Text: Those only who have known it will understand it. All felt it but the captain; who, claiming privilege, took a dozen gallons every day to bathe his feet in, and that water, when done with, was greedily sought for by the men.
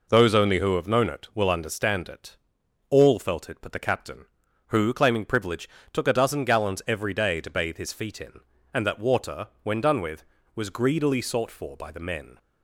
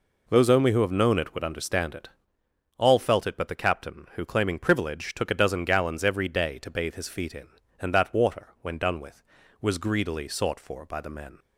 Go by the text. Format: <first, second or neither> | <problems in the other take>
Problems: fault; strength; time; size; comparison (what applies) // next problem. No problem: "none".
first | says "would" for "will"; at 1.3 s